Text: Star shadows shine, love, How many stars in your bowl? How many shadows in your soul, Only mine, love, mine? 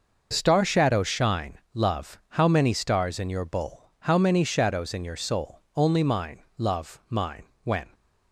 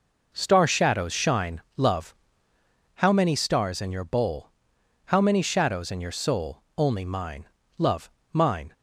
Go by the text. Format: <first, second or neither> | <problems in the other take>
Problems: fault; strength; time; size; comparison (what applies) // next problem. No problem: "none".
second | goes on to say "When"; slight; from 7.6 s on; 0.28 s long